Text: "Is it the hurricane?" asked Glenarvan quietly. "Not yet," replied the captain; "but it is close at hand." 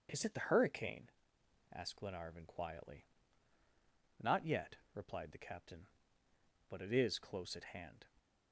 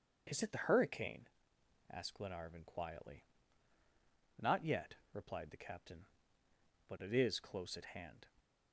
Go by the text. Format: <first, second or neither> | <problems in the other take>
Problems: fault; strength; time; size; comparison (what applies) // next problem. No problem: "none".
neither | starts louder than the rest; the same in both